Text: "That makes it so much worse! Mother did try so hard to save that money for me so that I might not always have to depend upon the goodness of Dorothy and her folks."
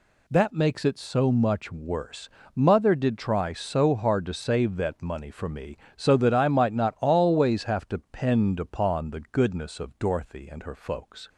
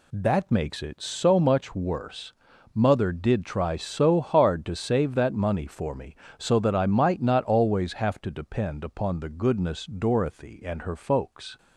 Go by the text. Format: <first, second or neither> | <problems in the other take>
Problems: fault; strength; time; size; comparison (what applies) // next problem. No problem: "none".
first | skips "of"; at 9.8 s